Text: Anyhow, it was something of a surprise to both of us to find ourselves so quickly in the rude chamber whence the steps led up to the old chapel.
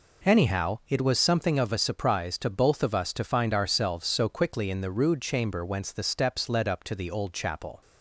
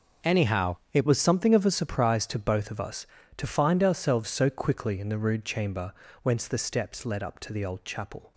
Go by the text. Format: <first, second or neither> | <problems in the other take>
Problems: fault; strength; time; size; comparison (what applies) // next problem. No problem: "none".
first | starts louder than the rest; noticeable; until 1.4 s; 6 dB // changes voice at "was"; from 1.0 s on; 7.3 s long // pauses between "chamber" and "whence"; slight; at 5.9 s; 0.28 s long